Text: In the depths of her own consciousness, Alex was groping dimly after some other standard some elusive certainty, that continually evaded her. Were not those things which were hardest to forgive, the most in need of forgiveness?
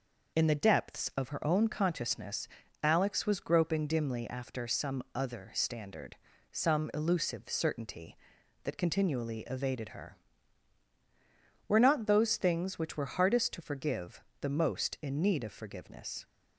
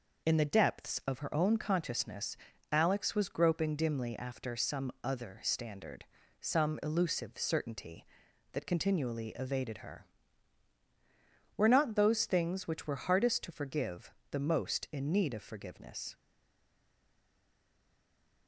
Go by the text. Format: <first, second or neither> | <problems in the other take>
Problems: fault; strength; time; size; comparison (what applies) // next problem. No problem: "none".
first | pauses between "standard" and "some"; slight; at 6.0 s; 0.36 s long; slight in the first // stays silent after the last word; from 16.1 s on; 2.3 s long